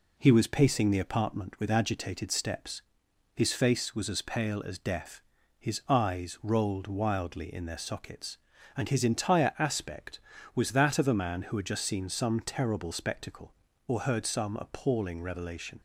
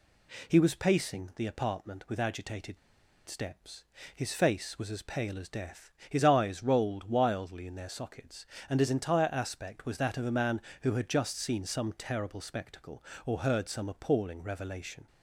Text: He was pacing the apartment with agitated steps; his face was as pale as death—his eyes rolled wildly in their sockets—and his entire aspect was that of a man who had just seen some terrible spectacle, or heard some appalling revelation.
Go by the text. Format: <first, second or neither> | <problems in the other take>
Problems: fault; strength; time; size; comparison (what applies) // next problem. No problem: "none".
first | pauses between "agitated" and "steps"; noticeable; at 2.7 s; 0.50 s long